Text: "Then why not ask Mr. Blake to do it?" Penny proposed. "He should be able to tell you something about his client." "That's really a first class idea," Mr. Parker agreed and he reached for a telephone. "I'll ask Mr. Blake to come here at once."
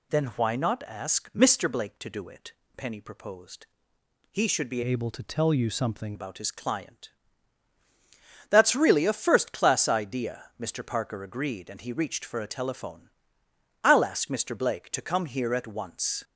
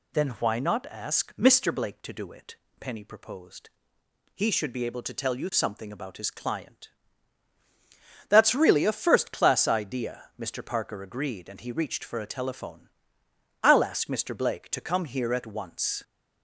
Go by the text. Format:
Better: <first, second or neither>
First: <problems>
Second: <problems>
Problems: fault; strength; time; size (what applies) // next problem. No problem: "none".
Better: second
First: changes voice from "able" to "something"; from 4.8 to 6.1 s; 1.3 s long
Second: none